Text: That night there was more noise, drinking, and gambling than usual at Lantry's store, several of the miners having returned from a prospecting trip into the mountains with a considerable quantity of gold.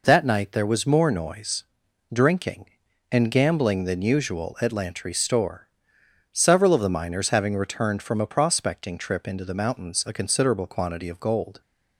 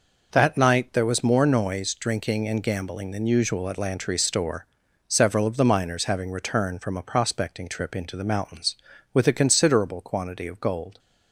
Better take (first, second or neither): second